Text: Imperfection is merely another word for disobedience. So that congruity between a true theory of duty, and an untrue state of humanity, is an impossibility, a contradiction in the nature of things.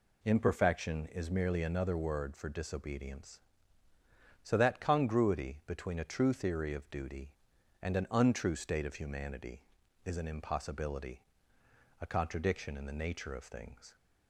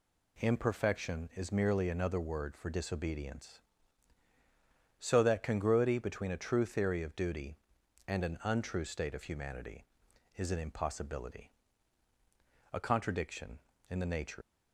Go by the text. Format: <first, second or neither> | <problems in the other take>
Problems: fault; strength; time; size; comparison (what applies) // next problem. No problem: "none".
first | stops before "of things"; at 14.4 s